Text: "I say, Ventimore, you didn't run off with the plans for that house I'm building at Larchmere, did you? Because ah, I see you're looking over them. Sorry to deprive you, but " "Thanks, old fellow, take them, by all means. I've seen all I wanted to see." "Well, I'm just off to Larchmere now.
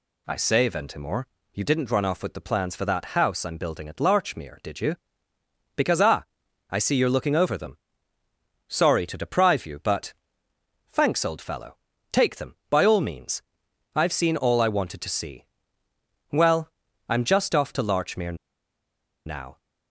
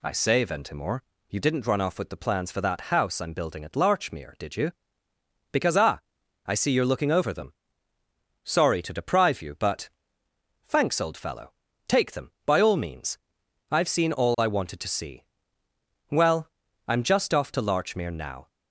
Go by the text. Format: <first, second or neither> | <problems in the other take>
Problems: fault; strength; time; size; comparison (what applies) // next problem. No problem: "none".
second | pauses between "Larchmere" and "now"; noticeable; at 18.3 s; 0.91 s long